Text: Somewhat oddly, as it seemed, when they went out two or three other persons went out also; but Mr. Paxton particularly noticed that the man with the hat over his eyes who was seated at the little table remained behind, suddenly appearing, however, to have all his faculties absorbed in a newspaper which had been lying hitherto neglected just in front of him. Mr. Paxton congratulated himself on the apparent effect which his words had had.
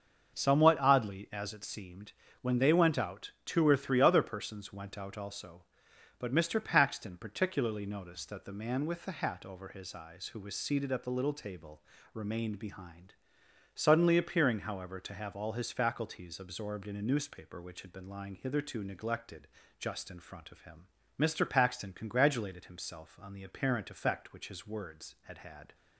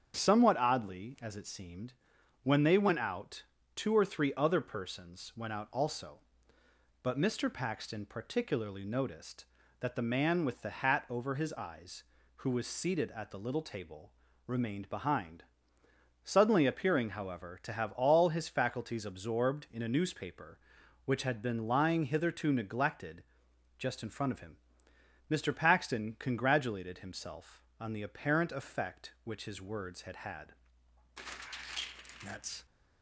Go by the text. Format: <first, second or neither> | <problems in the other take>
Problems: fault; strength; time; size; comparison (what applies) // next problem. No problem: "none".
first | starts louder than the rest; strong; until 1.1 s; 7.5 dB; also in the first // pauses between "out" and "two"; slight; at 3.4 s; 0.32 s long // pauses between "table" and "remained"; slight; at 14.1 s; 0.34 s long; slight in the first // pauses between "neglected" and "just"; noticeable; at 23.2 s; 0.56 s long; slight in the first // goes on to say "That's"; slight; from 32.2 s on; 0.42 s long